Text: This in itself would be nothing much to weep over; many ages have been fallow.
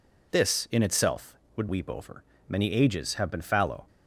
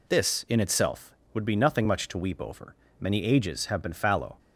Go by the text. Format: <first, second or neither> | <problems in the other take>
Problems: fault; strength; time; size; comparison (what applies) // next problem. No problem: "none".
second | skips "be nothing much to"; at 1.6 s